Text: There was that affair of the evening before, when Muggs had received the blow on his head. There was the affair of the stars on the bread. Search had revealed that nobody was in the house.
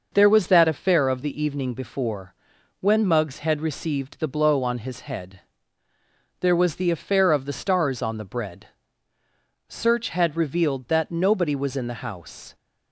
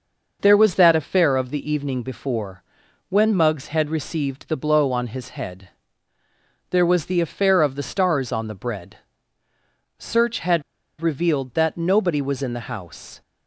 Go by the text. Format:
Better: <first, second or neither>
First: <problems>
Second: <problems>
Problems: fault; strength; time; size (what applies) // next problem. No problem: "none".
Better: first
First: none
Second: pauses between "had" and "revealed"; at 10.6 s; 0.38 s long